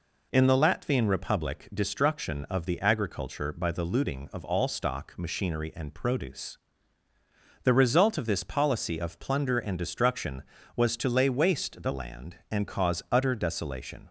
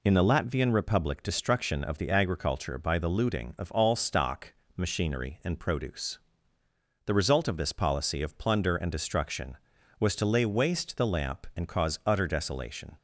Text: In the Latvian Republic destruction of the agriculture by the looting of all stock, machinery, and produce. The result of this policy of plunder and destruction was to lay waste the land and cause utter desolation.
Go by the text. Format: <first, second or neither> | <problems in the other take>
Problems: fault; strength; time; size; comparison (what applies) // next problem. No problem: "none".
first | says "lamp" for "land"; at 11.0 s